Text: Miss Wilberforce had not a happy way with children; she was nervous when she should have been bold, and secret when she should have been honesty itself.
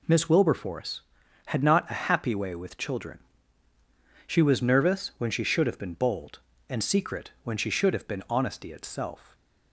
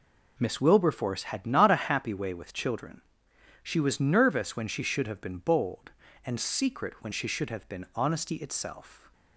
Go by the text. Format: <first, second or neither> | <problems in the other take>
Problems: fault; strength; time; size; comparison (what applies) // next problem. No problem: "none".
neither | none